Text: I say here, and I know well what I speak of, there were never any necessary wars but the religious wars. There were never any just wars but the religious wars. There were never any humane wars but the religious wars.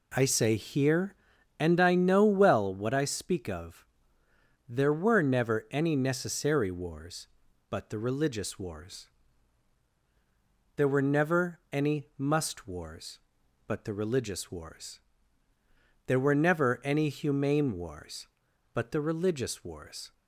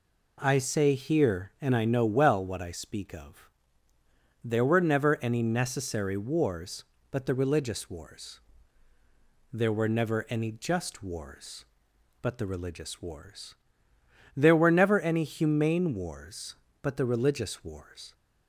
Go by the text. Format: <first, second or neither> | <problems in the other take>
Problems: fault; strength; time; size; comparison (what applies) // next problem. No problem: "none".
second | says "must" for "just"; at 12.1 s